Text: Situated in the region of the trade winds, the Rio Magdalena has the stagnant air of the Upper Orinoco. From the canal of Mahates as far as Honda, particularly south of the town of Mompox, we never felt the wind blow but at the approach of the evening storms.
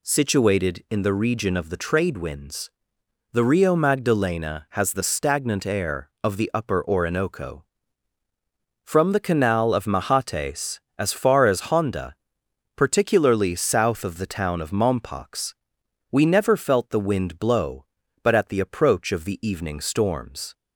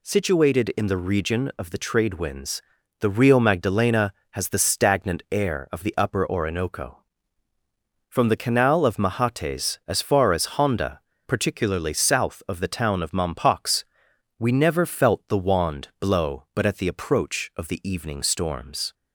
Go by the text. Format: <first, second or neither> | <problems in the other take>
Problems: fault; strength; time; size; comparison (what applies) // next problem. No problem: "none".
first | says "wand" for "wind"; at 15.3 s